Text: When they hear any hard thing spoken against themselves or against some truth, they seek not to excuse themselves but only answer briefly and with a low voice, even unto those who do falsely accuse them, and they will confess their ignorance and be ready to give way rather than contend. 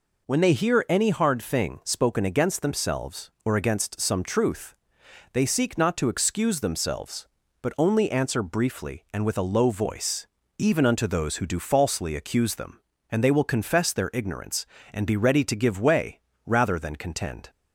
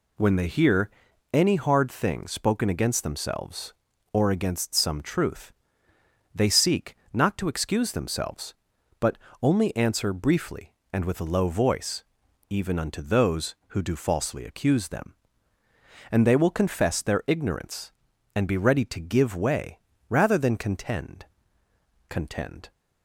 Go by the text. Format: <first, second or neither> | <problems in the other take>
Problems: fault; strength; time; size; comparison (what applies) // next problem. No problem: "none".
first | pauses between "hear" and "any"; at 0.8 s; 0.42 s long // pauses between "seek" and "not"; slight; at 6.9 s; 0.18 s long // pauses between "but" and "only"; slight; at 9.1 s; 0.24 s long // pauses between "way" and "rather"; slight; at 19.7 s; 0.32 s long; slight in the first // says "contend" twice; at 22.0 s